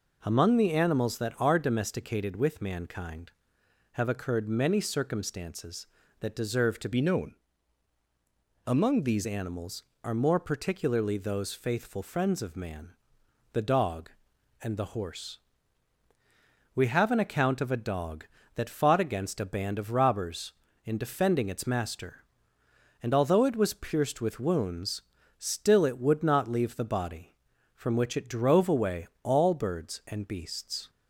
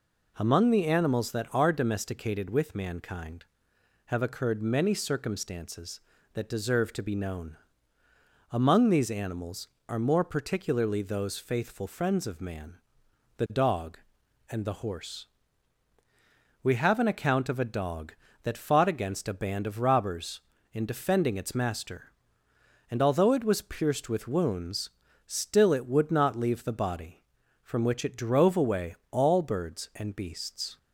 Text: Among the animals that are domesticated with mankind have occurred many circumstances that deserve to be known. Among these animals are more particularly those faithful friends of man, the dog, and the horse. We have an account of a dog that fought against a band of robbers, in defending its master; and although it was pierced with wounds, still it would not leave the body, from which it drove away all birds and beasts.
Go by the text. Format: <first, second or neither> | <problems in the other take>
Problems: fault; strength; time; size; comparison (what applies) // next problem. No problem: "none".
second | changes voice from "be" to "these"; from 6.9 to 9.2 s; 2.3 s long // pauses between "away" and "all"; slight; at 29.0 s; 0.18 s long; slight in the second